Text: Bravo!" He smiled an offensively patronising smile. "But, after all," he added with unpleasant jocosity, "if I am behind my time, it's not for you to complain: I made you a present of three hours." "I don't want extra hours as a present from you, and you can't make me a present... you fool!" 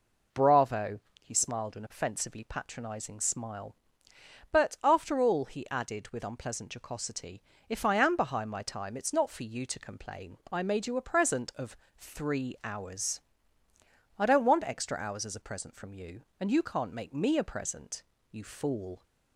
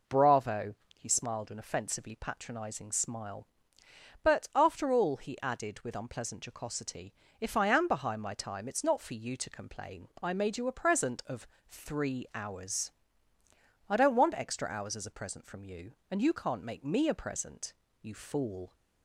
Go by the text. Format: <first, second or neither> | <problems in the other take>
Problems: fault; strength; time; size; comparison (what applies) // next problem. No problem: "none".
neither | pauses between "of" and "three"; slight; the same in both